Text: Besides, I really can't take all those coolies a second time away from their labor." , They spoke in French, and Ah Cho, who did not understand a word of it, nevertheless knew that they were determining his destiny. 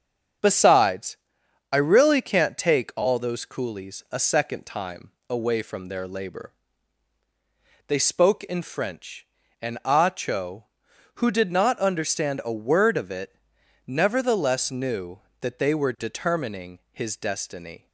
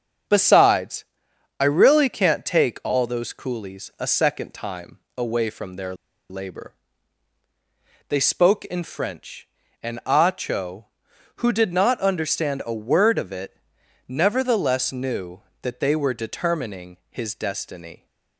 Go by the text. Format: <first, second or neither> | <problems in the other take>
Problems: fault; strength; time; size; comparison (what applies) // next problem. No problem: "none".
first | starts louder than the rest; until 1.8 s; 7 dB; also in the first // pauses between "time" and "away"; slight; at 4.9 s; 0.18 s long; slight in the first // pauses between "their" and "labor"; slight; at 5.9 s; 0.33 s long